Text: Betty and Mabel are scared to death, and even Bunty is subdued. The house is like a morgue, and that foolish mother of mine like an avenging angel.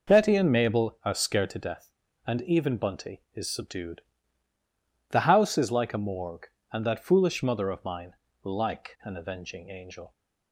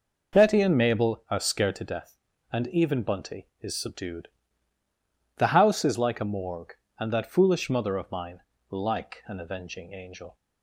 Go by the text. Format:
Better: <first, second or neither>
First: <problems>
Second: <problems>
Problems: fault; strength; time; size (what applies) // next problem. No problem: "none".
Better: neither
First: pauses between "mine" and "like"; slight; at 8.1 s; 0.28 s long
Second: pauses between "mine" and "like"; slight; at 8.4 s; 0.28 s long